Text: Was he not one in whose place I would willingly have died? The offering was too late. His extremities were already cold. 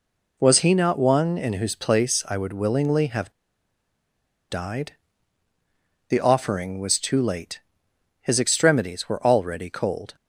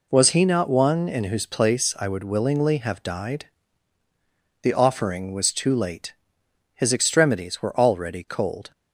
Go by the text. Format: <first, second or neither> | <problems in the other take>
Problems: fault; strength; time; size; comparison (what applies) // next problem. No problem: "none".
second | pauses between "have" and "died"; at 3.3 s; 1.1 s long